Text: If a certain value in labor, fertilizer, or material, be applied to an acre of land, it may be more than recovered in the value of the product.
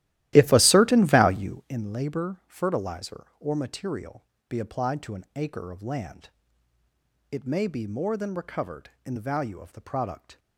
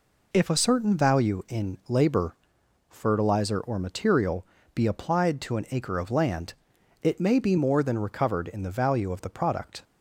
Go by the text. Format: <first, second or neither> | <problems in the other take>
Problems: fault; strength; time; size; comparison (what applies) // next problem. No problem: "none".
second | starts louder than the rest; strong; until 1.8 s; 15 dB